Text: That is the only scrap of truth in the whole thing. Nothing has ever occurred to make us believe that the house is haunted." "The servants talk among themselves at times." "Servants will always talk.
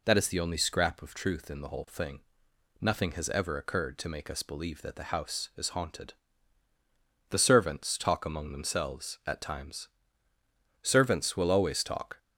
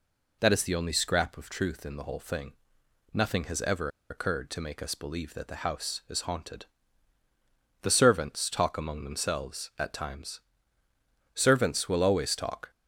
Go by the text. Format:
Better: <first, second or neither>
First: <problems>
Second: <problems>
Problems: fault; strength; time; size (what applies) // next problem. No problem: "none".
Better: first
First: none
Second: pauses between "ever" and "occurred"; slight; at 3.8 s; 0.21 s long